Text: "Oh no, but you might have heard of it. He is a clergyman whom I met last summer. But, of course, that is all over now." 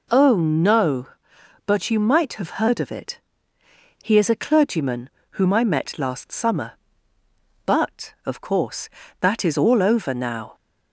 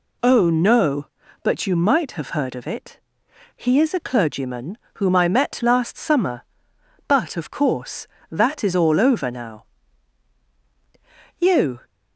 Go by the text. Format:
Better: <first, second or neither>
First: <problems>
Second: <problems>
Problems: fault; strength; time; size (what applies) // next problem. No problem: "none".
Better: first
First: pauses between "clergyman" and "whom"; slight; at 5.1 s; 0.20 s long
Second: pauses between "clergyman" and "whom"; slight; at 4.7 s; 0.18 s long // goes on to say "You"; slight; from 11.3 s on; 0.42 s long